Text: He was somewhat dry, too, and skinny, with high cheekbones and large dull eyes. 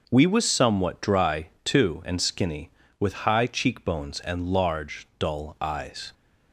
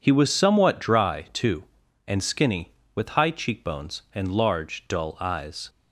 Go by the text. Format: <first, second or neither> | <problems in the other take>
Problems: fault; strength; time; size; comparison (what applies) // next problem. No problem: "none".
second | says "We" for "He"; at 0.1 s